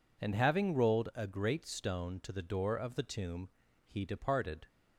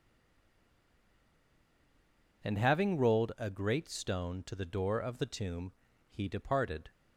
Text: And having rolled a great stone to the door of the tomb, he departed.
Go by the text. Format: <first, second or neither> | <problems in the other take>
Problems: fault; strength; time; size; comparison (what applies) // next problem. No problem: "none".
first | stays silent before the first word; until 2.4 s; 2.4 s long